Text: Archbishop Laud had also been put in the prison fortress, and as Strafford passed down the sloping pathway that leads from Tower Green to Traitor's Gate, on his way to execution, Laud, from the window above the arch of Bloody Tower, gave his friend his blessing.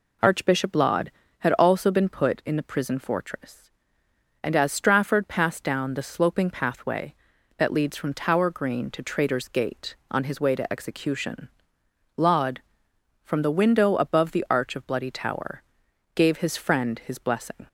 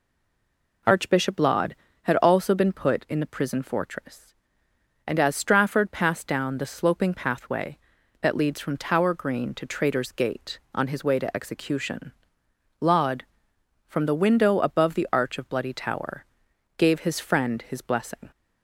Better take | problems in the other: first | stays silent before the first word; slight; until 0.8 s; 0.8 s long

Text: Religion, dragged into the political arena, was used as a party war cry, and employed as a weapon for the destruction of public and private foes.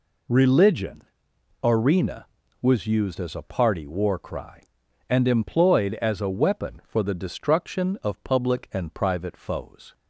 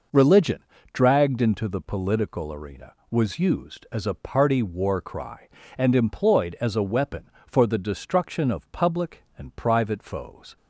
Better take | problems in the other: second | skips "dragged into the political"; at 1.3 s

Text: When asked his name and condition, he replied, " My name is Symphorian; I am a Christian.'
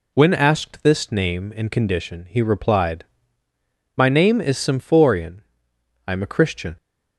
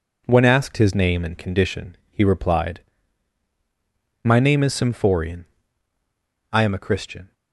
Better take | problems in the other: second | says "this" for "his"; at 0.8 s

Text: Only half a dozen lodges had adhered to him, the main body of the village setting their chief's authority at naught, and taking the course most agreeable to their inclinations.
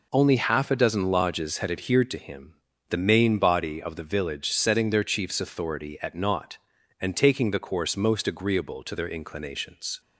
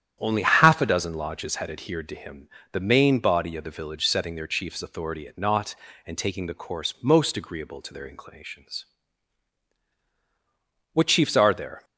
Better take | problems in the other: first | starts louder than the rest; strong; until 1.2 s; 10 dB // goes on to say "What chiefs are there"; noticeable; from 10.9 s on; 0.90 s long

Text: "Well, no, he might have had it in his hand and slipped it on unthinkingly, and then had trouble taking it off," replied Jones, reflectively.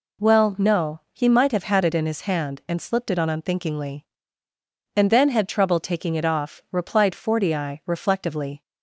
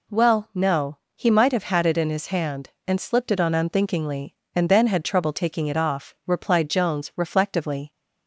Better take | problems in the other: second | says "Fortii" for "Jones"; at 7.1 s

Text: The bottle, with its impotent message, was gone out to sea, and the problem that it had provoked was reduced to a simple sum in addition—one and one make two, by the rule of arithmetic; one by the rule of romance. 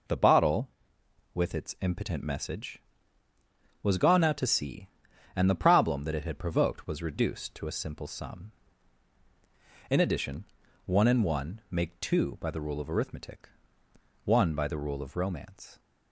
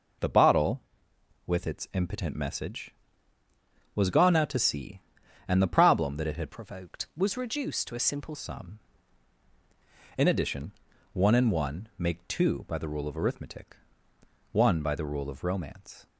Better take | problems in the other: first | changes voice from "provoked" to "simple"; from 6.4 to 8.3 s; 1.9 s long

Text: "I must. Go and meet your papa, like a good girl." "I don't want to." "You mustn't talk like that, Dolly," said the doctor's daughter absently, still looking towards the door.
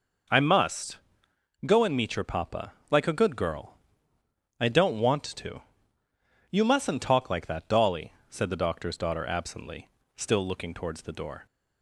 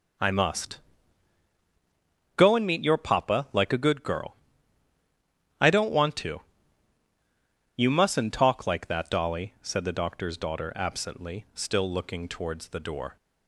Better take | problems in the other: neither | none

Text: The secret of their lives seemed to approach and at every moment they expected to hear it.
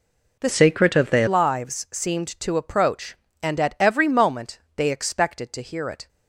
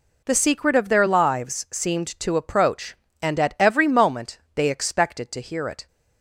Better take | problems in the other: second | changes voice from "secret" to "their"; from 0.4 to 1.2 s; 0.8 s long // pauses between "moment" and "they"; slight; at 4.5 s; 0.18 s long; slight in the second

